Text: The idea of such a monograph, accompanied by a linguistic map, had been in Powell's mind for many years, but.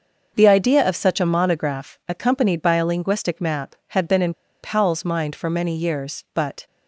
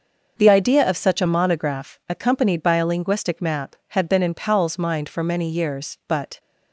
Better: second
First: starts louder than the rest; noticeable; until 1.3 s; 6 dB // pauses between "in" and "Powell's"; slight; at 4.3 s; 0.28 s long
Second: starts louder than the rest; until 1.4 s; 6 dB

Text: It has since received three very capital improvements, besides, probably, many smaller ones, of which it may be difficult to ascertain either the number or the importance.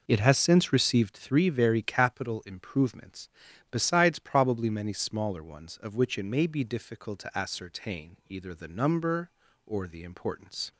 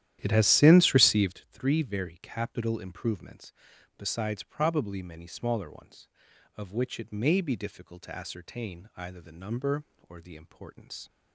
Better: first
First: none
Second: starts louder than the rest; strong; until 1.4 s; 12 dB

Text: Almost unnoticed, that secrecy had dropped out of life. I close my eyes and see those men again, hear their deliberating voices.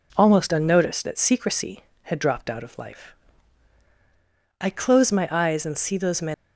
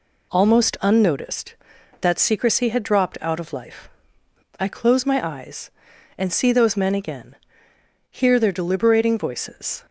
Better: second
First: stops before "again hear their deliberating voices"; at 6.3 s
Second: none

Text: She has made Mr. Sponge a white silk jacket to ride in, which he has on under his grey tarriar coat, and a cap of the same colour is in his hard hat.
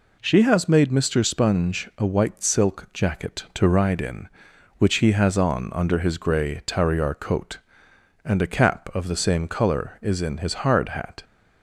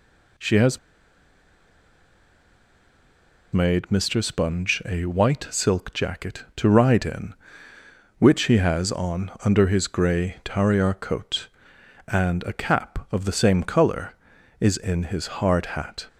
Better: first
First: none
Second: pauses between "has" and "made"; strong; at 0.7 s; 2.7 s long

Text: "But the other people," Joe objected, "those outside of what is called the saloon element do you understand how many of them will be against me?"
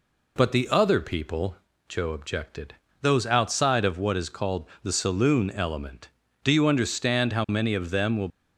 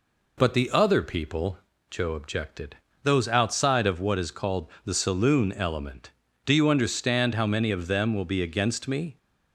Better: second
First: pauses between "called" and "the"; slight; at 4.6 s; 0.16 s long // stops before "be against me"; at 8.2 s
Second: pauses between "called" and "the"; slight; at 4.6 s; 0.16 s long

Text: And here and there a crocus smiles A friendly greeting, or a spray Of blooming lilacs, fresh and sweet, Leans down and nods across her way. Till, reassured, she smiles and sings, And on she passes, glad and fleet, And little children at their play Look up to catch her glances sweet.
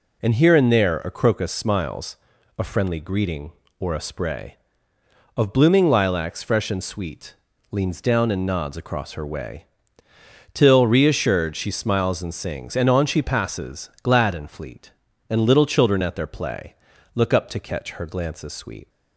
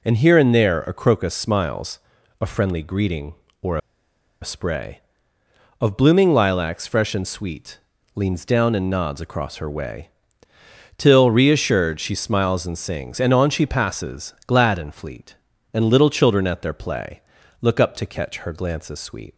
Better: first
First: pauses between "smiles" and "A"; at 2.1 s; 0.40 s long // pauses between "play" and "Look"; at 16.7 s; 0.40 s long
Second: pauses between "smiles" and "A"; at 1.9 s; 0.40 s long // pauses between "or" and "a"; noticeable; at 3.7 s; 0.63 s long // pauses between "play" and "Look"; at 17.2 s; 0.40 s long

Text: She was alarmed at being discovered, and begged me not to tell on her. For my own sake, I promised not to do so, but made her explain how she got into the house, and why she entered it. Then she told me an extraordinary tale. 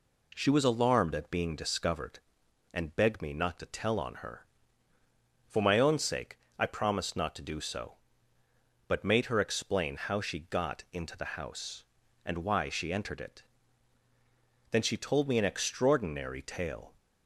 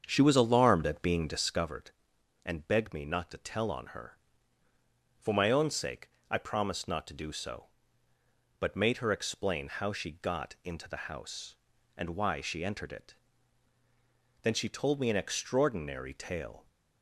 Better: first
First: none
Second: starts louder than the rest; strong; until 1.7 s; 7 dB

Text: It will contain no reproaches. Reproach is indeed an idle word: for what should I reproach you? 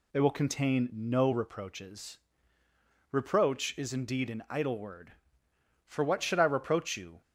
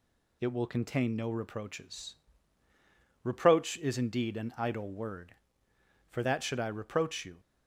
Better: first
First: none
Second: says "that" for "what"; at 6.2 s

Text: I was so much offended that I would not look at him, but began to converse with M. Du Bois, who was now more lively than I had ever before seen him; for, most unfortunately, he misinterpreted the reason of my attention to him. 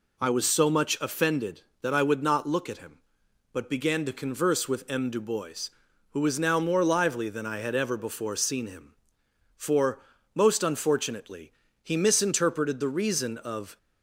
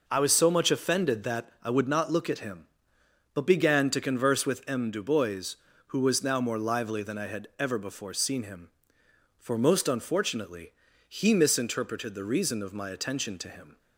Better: second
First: stops before "my attention to him"; at 13.7 s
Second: none

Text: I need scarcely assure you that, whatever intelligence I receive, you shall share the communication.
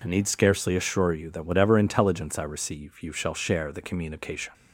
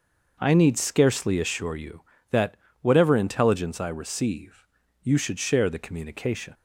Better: first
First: none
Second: starts louder than the rest; noticeable; until 1.4 s; 6 dB // says "should" for "shall"; at 5.1 s

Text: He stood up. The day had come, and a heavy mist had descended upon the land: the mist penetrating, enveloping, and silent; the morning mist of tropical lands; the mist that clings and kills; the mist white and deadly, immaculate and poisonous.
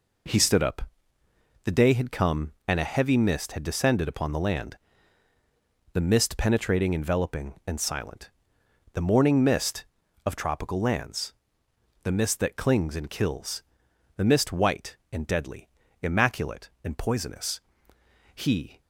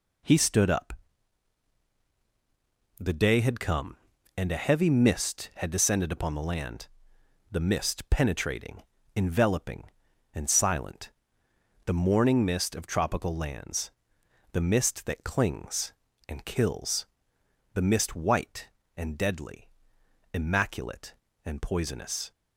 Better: second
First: goes on to say "He"; slight; from 18.3 s on; 0.46 s long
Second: none

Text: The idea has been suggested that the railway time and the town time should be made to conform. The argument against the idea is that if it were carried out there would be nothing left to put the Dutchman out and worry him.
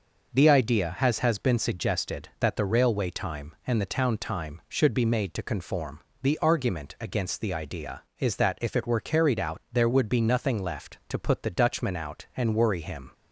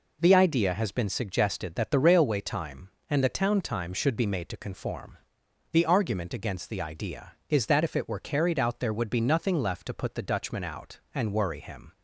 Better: second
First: says "has" twice; at 1.1 s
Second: none

